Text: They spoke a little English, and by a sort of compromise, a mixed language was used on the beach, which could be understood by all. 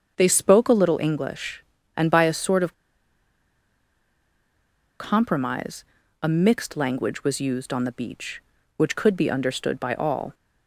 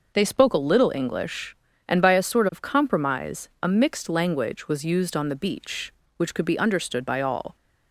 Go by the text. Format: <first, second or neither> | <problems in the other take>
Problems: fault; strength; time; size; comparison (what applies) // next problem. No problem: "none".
second | starts louder than the rest; until 1.1 s; 7 dB // pauses between "of" and "compromise"; strong; at 2.7 s; 2.2 s long